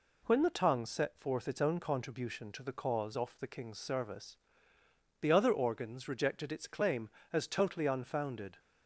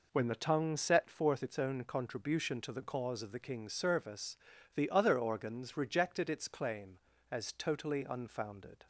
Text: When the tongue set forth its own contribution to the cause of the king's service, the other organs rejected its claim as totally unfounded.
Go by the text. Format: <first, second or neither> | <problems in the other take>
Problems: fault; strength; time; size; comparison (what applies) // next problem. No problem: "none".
second | says "off" for "of"; at 3.1 s